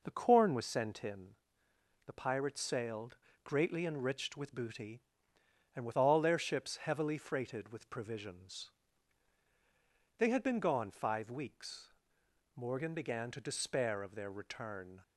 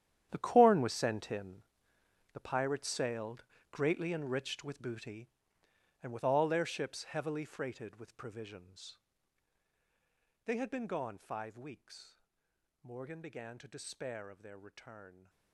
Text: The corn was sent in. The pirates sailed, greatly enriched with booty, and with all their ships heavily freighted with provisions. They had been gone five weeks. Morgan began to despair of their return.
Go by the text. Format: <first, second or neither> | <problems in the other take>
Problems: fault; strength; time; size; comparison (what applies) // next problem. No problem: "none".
first | gets quieter; strong; throughout; 15 dB